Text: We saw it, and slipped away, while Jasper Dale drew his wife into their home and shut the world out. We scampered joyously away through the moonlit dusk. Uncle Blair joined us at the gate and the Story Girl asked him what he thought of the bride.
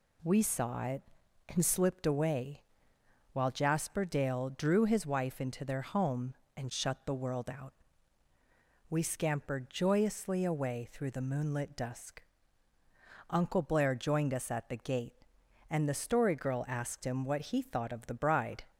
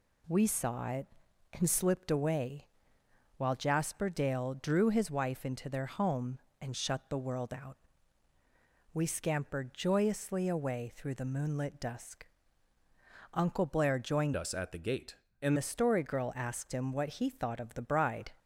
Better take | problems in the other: first | changes voice from "us" to "and"; from 14.3 to 15.5 s; 1.2 s long

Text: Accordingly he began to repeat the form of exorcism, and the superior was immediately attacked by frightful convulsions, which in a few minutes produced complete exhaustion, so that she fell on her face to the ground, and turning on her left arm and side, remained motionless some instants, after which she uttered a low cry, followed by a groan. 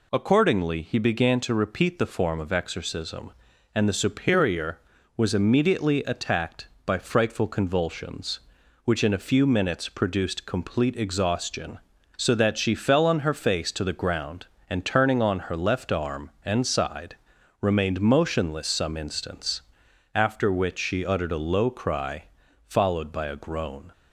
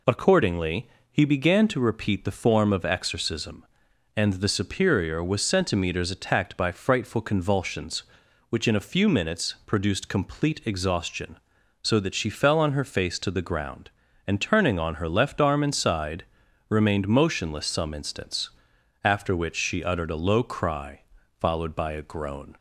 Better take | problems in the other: first | pauses between "Accordingly" and "he"; slight; at 0.8 s; 0.22 s long // says "centimeters" for "immediately"; at 5.4 s

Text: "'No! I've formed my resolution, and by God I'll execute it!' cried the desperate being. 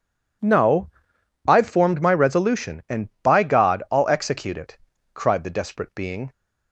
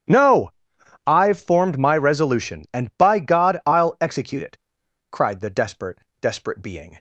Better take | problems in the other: first | starts louder than the rest; strong; until 1.6 s; 10 dB // says "desperate" twice; at 6.2 s

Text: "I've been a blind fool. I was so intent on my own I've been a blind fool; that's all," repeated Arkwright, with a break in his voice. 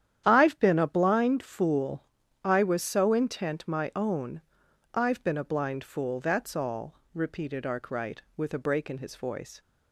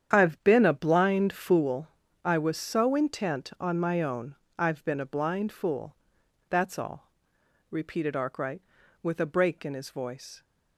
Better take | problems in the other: second | starts louder than the rest; strong; until 1.2 s; 10 dB; strong in the second // skips "on"; at 3.6 s // pauses between "own" and "I've"; noticeable; at 4.4 s; 0.54 s long; slight in the second

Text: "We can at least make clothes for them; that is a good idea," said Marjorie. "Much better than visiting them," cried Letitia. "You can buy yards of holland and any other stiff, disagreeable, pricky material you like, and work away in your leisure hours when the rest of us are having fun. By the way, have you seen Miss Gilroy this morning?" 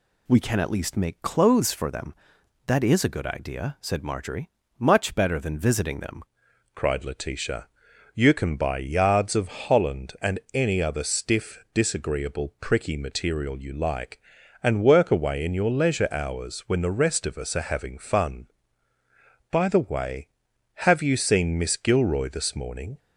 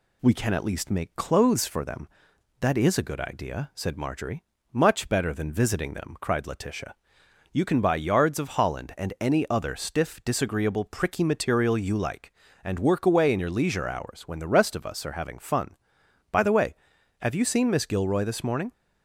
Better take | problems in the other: second | changes voice at "cried"; from 6.7 s on; 16.2 s long // pauses between "and" and "any"; slight; at 10.3 s; 0.16 s long

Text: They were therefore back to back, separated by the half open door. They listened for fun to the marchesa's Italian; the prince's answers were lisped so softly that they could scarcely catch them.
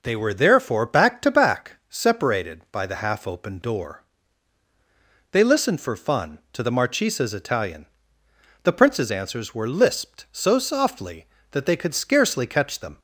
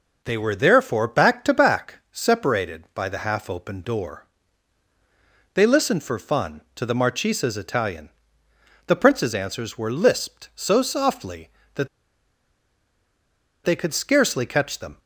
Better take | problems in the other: first | pauses between "that" and "they"; strong; at 11.8 s; 1.7 s long

